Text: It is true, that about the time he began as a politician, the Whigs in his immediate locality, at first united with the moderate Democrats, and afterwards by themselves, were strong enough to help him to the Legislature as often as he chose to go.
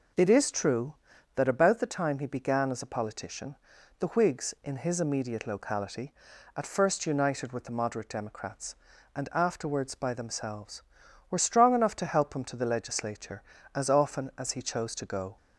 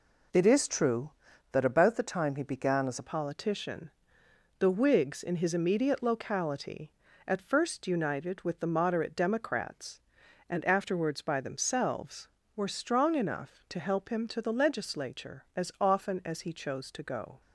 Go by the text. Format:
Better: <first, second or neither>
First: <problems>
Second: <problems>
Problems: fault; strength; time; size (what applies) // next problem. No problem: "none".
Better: first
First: none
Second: changes voice at "politician"; from 3.0 s on; 14.4 s long